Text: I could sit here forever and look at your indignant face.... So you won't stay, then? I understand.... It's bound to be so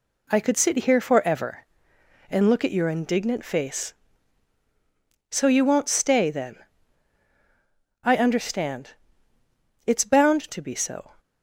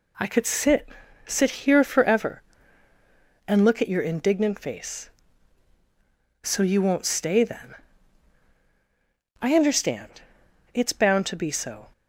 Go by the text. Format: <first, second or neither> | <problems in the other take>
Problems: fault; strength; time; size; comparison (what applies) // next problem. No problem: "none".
first | says "sit" twice; at 1.2 s